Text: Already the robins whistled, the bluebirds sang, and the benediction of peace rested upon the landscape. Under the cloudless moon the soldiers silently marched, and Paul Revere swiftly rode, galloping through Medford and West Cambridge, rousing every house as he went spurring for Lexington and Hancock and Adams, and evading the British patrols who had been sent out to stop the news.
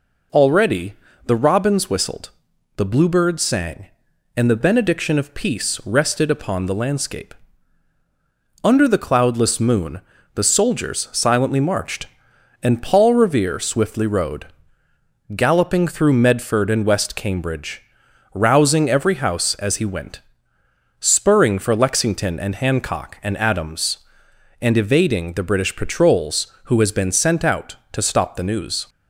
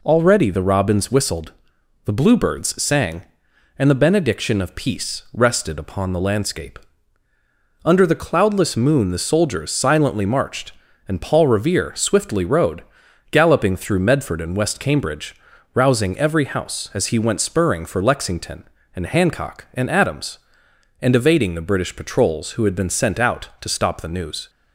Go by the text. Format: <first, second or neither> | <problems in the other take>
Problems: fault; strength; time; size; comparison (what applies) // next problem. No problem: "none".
second | pauses between "Already" and "the"; slight; at 0.9 s; 0.32 s long // pauses between "moon" and "the"; slight; at 10.0 s; 0.32 s long // pauses between "went" and "spurring"; noticeable; at 20.1 s; 0.80 s long // says "has" for "had"; at 26.7 s